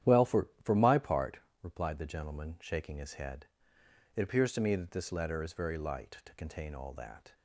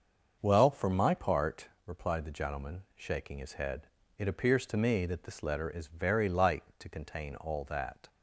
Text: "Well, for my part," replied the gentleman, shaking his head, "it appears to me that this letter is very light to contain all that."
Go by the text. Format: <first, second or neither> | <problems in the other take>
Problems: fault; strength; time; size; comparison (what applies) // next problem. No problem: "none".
second | starts louder than the rest; strong; until 1.2 s; 11 dB; also in the second // says "for" twice; at 0.6 s